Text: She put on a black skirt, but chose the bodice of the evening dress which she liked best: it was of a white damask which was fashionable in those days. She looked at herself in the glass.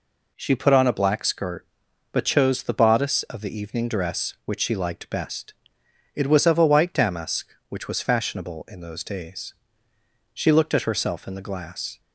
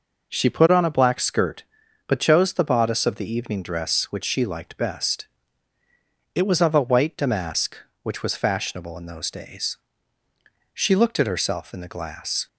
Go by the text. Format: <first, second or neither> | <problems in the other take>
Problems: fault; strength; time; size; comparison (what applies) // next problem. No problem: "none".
neither | none